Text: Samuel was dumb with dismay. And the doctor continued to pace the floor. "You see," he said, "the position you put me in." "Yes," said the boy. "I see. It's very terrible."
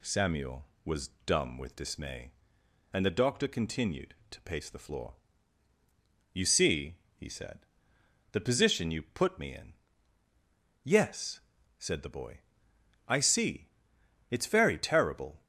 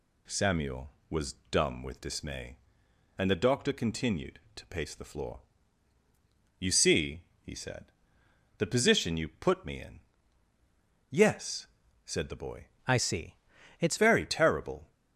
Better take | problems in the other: first | pauses between "was" and "dumb"; slight; at 1.3 s; 0.18 s long; slight in the first // changes voice from "I" to "It's"; from 12.8 to 13.9 s; 1.1 s long

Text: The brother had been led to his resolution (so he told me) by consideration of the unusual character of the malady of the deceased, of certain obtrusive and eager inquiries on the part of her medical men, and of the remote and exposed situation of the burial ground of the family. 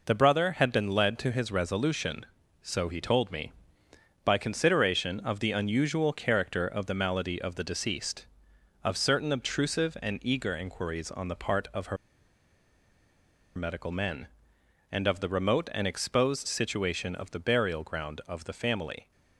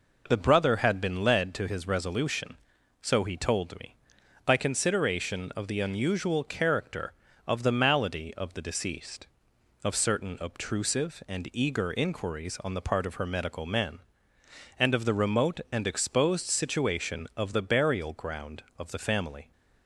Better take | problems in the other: second | pauses between "her" and "medical"; strong; at 11.9 s; 1.6 s long

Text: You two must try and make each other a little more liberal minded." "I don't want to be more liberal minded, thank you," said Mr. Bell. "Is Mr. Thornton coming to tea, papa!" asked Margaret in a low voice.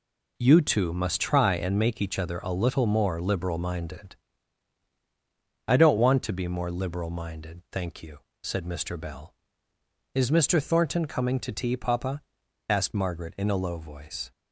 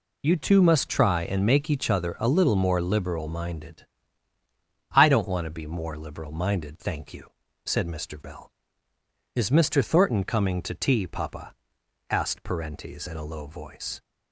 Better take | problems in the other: first | says "Parentes" for "Margaret"; at 12.4 s

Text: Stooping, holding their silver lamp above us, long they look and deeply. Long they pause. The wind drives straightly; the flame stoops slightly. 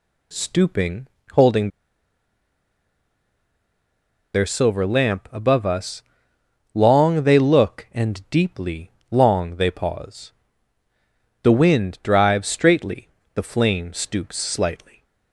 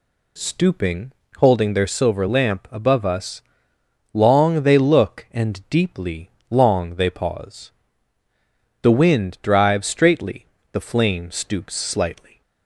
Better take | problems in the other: second | pauses between "holding" and "their"; strong; at 1.6 s; 2.6 s long

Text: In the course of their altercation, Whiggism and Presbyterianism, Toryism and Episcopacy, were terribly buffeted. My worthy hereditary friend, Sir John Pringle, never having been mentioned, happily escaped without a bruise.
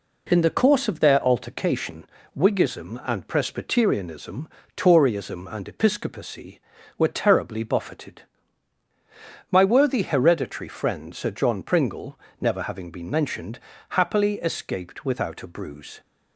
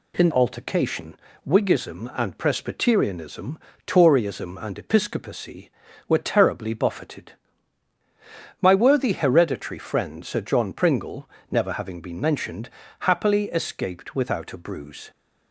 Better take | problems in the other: first | skips "the course of their"; at 0.3 s

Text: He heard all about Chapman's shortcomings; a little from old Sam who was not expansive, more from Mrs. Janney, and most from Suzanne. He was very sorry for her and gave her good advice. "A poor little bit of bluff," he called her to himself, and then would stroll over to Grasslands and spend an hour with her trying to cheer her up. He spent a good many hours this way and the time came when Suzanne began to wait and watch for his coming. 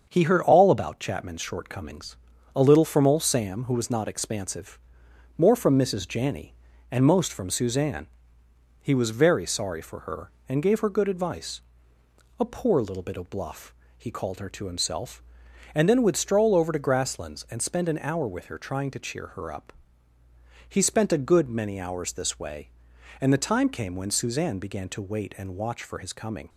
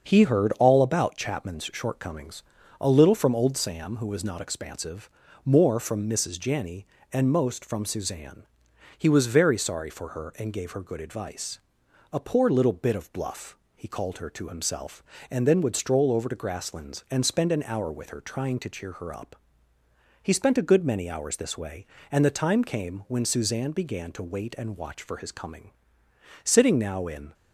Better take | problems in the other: first | starts louder than the rest; until 1.1 s; 6.5 dB; also in the first // goes on to say "Sitting now in"; noticeable; from 26.4 s on; 0.90 s long

